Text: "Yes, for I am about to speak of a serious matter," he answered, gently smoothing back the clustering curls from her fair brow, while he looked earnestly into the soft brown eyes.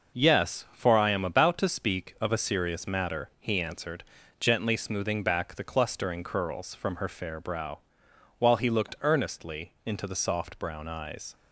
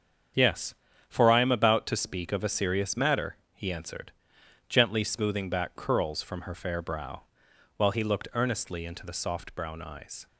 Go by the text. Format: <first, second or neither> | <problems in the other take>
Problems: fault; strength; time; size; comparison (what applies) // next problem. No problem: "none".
first | starts louder than the rest; strong; until 1.6 s; 7.5 dB // skips "the clustering"; at 5.7 s